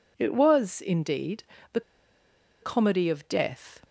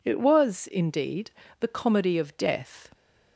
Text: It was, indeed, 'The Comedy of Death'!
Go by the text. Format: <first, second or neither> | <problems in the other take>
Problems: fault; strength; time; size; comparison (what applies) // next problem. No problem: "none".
second | pauses between "The" and "Comedy"; noticeable; at 1.8 s; 0.81 s long